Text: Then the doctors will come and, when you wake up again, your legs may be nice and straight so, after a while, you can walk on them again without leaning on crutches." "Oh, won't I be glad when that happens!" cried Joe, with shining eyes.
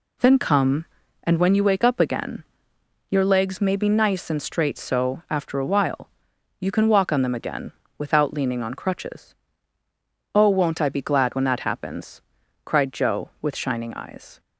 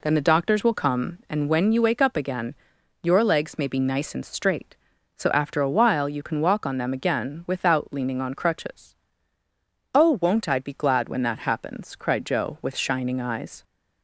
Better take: second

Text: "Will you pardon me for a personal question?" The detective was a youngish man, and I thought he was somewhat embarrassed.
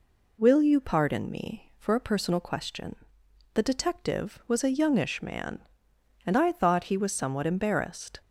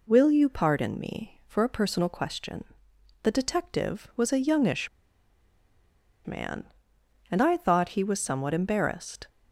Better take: first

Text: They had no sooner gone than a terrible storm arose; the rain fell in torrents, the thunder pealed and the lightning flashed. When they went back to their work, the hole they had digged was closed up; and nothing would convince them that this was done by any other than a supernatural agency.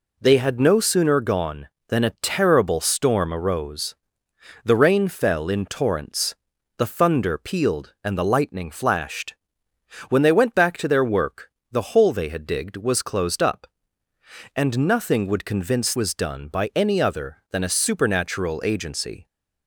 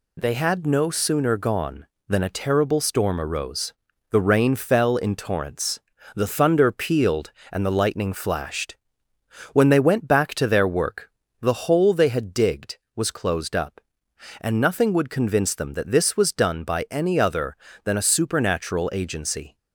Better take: second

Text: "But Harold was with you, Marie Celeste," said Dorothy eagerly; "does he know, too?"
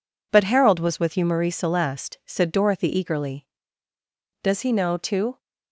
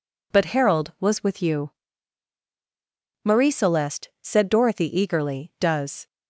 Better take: first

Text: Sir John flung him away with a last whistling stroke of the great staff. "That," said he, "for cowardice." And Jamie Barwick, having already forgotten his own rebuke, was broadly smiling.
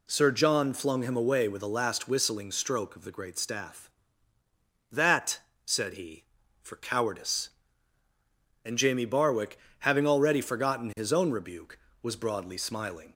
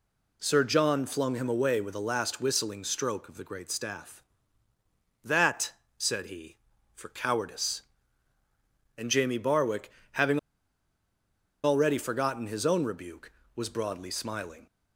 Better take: first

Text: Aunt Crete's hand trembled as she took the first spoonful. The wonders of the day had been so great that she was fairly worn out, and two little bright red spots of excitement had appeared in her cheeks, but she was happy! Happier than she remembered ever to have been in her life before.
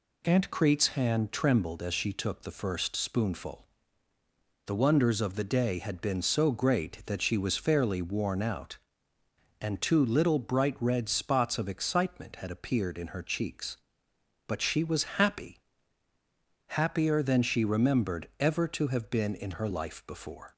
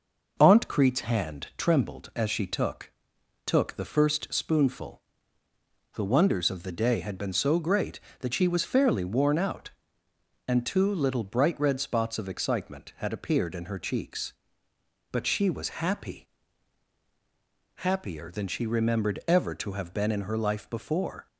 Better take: first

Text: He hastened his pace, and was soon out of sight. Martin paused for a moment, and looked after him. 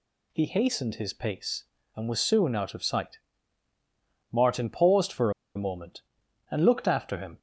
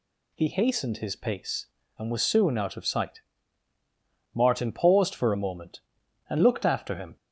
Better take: second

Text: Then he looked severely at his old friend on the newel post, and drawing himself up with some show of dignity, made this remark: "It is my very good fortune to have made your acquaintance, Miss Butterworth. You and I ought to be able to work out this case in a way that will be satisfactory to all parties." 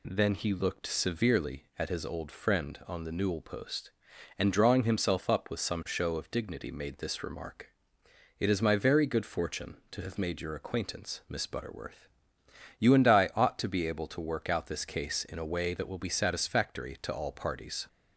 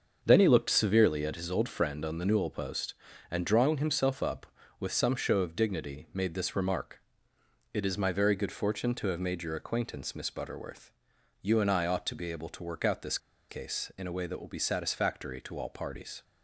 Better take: first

